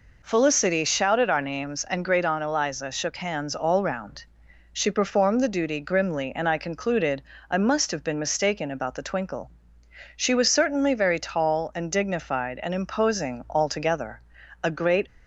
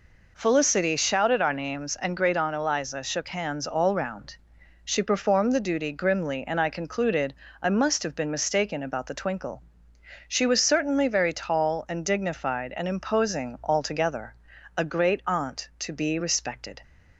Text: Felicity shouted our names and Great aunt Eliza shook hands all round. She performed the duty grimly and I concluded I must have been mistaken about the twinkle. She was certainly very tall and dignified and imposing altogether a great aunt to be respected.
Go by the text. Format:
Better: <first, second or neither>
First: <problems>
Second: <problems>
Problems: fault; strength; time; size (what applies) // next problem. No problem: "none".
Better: second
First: pauses between "concluded" and "I"; slight; at 7.2 s; 0.26 s long // pauses between "altogether" and "a"; at 14.2 s; 0.42 s long // stops before "aunt to be respected"; at 15.0 s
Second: pauses between "concluded" and "I"; slight; at 7.3 s; 0.26 s long // pauses between "altogether" and "a"; at 14.3 s; 0.42 s long